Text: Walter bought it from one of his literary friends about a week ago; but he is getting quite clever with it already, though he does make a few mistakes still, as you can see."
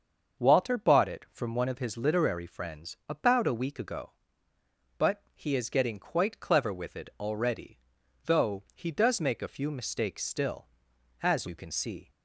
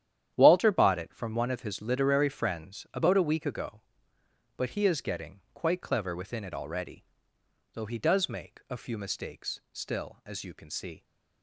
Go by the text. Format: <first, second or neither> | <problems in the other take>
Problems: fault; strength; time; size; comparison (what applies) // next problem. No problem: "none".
first | starts louder than the rest; strong; until 1.3 s; 10.5 dB; also in the first // says "within" for "with"; at 6.1 s